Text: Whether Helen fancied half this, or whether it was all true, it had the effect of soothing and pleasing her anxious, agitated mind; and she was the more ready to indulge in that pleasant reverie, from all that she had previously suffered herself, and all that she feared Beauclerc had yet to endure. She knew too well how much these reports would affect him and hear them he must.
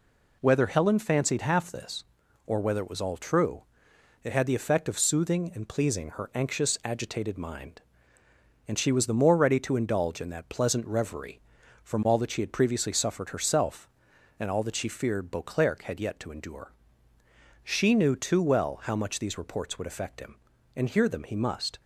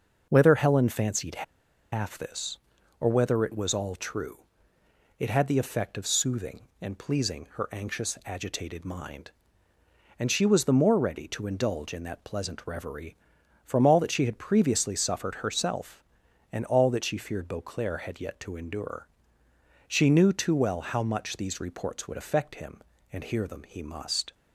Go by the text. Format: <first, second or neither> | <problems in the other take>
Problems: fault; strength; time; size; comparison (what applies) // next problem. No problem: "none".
first | pauses between "fancied" and "half"; noticeable; at 1.4 s; 0.49 s long